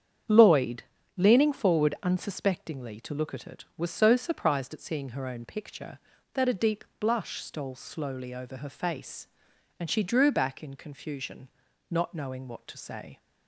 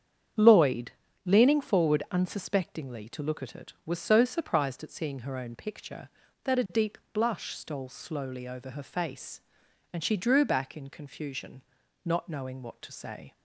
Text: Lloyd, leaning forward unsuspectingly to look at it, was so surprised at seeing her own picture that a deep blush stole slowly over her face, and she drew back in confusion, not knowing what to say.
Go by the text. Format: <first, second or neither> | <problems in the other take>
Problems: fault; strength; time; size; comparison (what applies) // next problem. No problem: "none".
neither | starts louder than the rest; strong; the same in both // pauses between "deep" and "blush"; slight; the same in both